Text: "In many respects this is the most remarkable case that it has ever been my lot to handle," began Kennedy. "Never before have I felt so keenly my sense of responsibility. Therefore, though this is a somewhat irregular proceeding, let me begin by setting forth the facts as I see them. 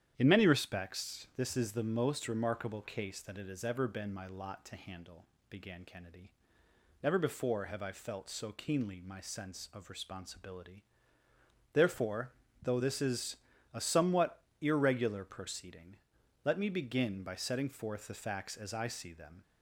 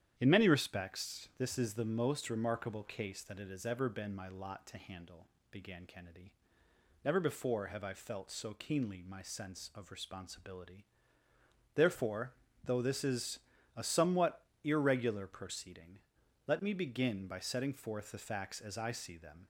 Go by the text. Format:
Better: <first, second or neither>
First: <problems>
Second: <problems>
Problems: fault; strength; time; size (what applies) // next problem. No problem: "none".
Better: neither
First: starts louder than the rest; strong; until 1.1 s; 10 dB // pauses between "is" and "a"; slight; at 13.3 s; 0.34 s long // pauses between "somewhat" and "irregular"; slight; at 14.3 s; 0.20 s long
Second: starts louder than the rest; strong; until 1.1 s; 10 dB // pauses between "is" and "a"; slight; at 13.4 s; 0.34 s long // pauses between "somewhat" and "irregular"; slight; at 14.4 s; 0.20 s long